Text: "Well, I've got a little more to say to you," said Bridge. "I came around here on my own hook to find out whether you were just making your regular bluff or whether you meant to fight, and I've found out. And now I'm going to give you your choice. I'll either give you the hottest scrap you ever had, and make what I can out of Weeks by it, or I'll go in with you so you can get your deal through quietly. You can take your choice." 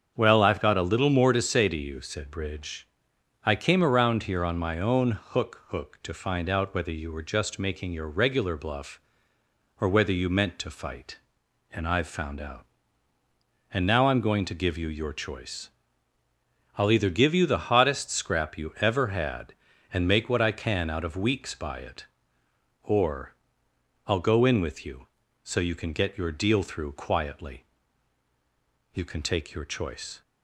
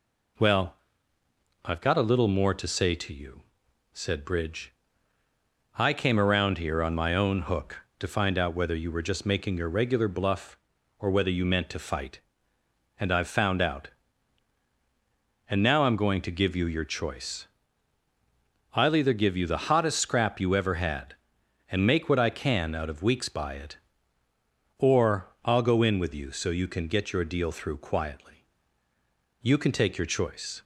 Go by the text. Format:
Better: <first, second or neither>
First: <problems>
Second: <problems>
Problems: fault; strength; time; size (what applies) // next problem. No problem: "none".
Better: second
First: starts louder than the rest; strong; until 1.1 s; 7 dB // says "hook" twice; at 5.6 s // pauses between "or" and "I'll"; noticeable; at 23.3 s; 0.72 s long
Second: none